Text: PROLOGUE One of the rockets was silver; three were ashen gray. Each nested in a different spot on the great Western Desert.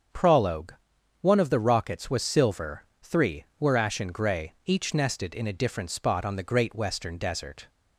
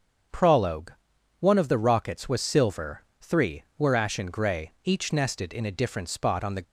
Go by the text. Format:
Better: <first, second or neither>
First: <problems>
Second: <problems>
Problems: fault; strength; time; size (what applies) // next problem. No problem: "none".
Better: first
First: starts louder than the rest; strong; until 1.5 s; 7 dB // pauses between "PROLOGUE" and "One"; noticeable; at 0.7 s; 0.46 s long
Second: starts louder than the rest; until 1.7 s; 7 dB // pauses between "PROLOGUE" and "One"; noticeable; at 0.9 s; 0.46 s long // stops before "great Western Desert"; at 6.6 s